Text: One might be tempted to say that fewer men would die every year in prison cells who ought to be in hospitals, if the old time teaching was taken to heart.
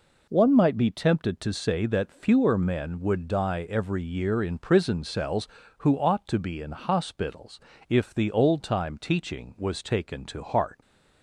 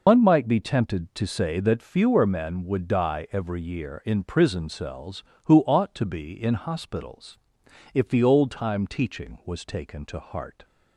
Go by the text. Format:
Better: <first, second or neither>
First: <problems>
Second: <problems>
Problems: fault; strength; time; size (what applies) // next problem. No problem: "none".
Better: first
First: none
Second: loses the start of "One"; at 0.0 s; 125 ms